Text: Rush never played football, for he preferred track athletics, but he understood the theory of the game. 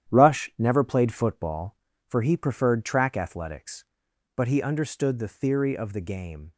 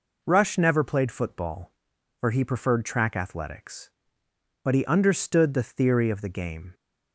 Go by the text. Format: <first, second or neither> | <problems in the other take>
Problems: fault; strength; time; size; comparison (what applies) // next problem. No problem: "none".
second | gets quieter; strong; throughout; 8.5 dB